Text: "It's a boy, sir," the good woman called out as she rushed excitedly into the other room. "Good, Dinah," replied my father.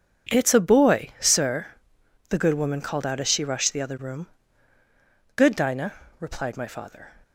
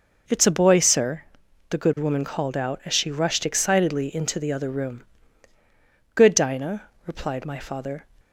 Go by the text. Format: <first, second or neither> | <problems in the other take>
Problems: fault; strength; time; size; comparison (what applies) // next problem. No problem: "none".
second | skips "excitedly into"; at 3.7 s